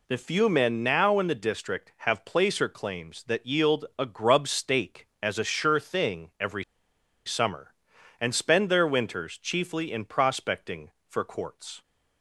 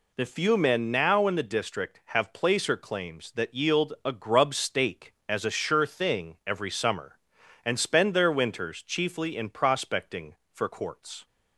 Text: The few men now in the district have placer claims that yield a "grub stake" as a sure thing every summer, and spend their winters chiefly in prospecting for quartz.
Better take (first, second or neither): second